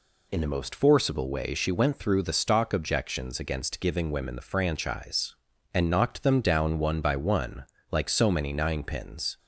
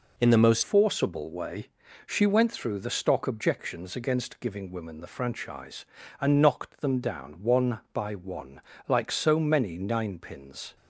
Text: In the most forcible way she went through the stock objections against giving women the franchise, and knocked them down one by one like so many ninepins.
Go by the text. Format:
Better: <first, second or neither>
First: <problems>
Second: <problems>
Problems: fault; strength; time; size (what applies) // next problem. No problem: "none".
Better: first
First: pauses between "one" and "like"; slight; at 7.6 s; 0.25 s long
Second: changes voice at "forcible"; from 0.6 s on; 10.1 s long // pauses between "way" and "she"; slight; at 1.6 s; 0.36 s long // pauses between "one" and "like"; slight; at 8.6 s; 0.26 s long